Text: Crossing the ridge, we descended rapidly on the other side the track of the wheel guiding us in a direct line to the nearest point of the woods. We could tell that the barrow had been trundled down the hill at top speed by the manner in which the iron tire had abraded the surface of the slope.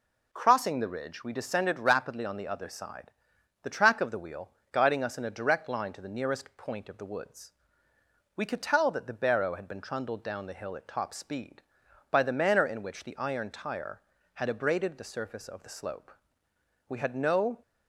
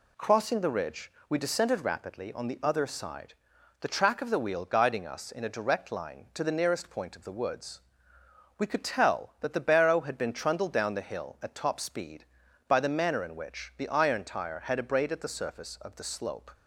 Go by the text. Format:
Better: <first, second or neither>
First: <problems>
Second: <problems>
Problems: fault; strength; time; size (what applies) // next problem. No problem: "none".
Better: second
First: pauses between "side" and "the"; noticeable; at 3.1 s; 0.52 s long // pauses between "wheel" and "guiding"; slight; at 4.4 s; 0.22 s long // goes on to say "We had no"; noticeable; from 16.8 s on; 0.74 s long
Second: pauses between "side" and "the"; noticeable; at 3.3 s; 0.46 s long